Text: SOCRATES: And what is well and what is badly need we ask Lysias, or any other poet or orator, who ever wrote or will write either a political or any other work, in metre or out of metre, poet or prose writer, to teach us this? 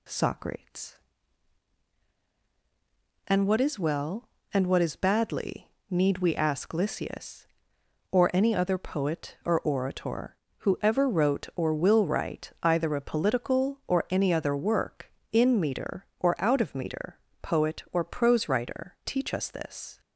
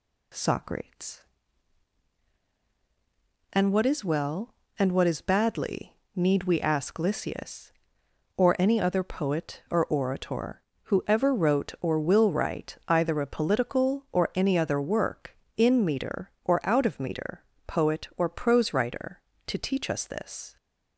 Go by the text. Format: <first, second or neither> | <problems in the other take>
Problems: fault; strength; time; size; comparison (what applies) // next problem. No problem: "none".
second | pauses between "badly" and "need"; slight; at 5.6 s; 0.20 s long; slight in the second // skips "to"; at 19.0 s